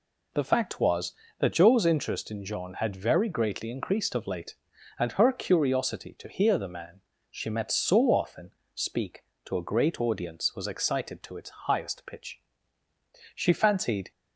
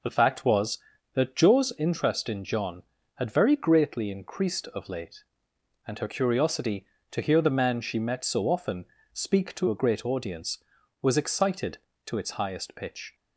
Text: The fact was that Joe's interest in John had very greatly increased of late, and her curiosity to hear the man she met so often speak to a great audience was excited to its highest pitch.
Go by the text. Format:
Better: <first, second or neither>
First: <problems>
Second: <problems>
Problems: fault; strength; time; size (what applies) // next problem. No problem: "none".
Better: second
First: pauses between "man" and "she"; slight; at 7.0 s; 0.30 s long // pauses between "often" and "speak"; slight; at 8.5 s; 0.24 s long // goes on to say "She fancied"; noticeable; from 13.3 s on; 0.76 s long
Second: pauses between "often" and "speak"; slight; at 8.8 s; 0.28 s long